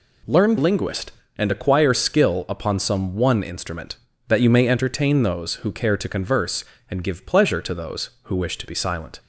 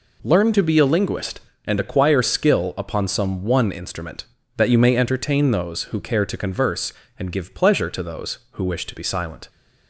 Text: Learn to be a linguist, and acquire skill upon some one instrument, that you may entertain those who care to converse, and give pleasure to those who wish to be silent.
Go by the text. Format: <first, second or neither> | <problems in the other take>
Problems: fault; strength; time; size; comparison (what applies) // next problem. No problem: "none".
second | skips "to be a"; at 0.5 s